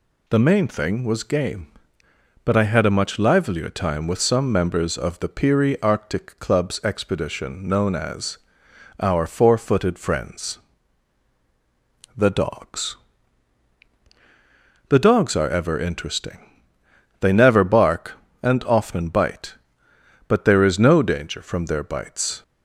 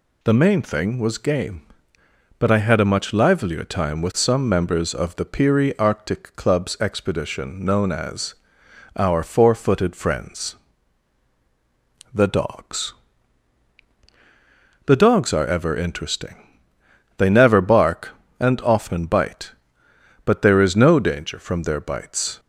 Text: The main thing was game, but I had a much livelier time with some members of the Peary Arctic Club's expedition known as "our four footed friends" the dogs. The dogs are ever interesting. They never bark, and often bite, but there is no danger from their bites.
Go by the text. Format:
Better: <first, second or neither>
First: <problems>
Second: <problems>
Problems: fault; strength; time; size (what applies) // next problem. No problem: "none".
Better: neither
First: pauses between "as" and "our"; noticeable; at 8.3 s; 0.62 s long // pauses between "friends" and "the"; strong; at 10.5 s; 1.5 s long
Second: pauses between "as" and "our"; noticeable; at 8.3 s; 0.62 s long // pauses between "friends" and "the"; strong; at 10.5 s; 1.5 s long